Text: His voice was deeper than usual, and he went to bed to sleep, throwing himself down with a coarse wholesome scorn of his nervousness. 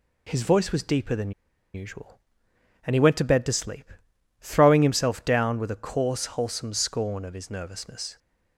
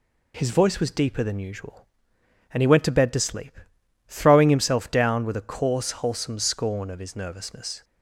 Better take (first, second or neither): second